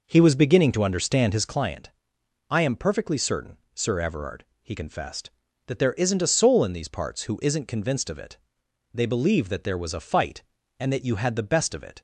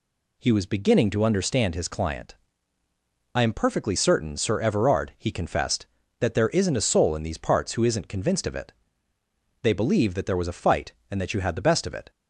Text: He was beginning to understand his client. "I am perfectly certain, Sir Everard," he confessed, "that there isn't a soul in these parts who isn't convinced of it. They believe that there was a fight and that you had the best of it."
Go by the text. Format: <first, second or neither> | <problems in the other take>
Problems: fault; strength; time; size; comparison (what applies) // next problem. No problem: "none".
second | starts louder than the rest; noticeable; until 1.6 s; 5 dB